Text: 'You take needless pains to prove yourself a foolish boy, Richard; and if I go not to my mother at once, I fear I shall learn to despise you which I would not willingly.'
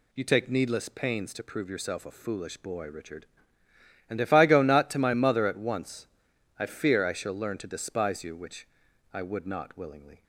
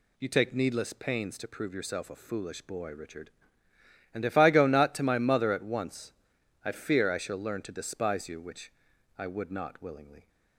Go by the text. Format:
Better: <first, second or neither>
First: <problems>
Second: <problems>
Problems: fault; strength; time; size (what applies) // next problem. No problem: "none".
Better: neither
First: pauses between "which" and "I"; noticeable; at 8.6 s; 0.46 s long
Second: pauses between "which" and "I"; noticeable; at 8.7 s; 0.46 s long